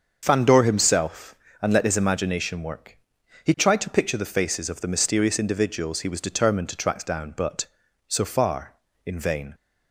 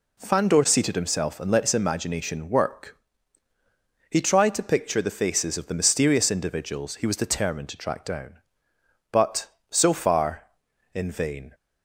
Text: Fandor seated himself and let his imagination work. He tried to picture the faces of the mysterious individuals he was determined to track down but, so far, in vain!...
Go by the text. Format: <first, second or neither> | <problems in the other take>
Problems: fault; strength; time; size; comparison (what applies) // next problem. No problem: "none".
second | starts louder than the rest; until 1.2 s; 6.5 dB // skips "seated"; at 0.6 s